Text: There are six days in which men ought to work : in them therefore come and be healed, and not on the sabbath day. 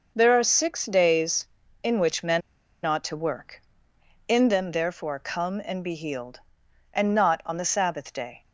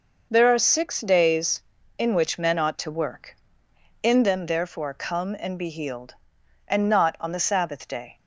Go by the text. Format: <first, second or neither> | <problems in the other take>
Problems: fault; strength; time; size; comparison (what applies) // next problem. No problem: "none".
second | pauses between "men" and "ought"; at 2.4 s; 0.44 s long